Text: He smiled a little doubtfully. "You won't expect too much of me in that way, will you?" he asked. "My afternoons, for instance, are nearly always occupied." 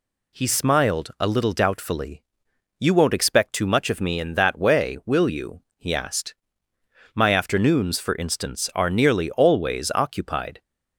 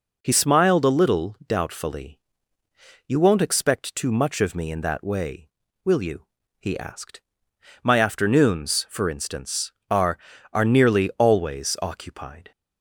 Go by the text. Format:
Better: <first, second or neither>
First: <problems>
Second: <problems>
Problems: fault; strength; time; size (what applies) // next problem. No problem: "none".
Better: first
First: none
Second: says "are" twice; at 10.5 s